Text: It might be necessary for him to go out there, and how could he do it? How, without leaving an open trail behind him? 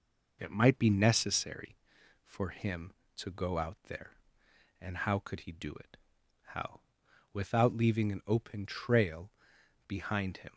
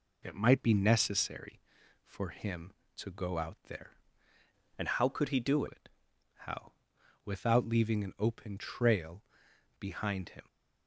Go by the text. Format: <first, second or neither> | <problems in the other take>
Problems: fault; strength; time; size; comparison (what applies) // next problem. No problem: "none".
first | changes voice from "and" to "do"; from 4.7 to 5.6 s; 0.9 s long // pauses between "trail" and "behind"; noticeable; at 9.2 s; 0.56 s long; noticeable in the first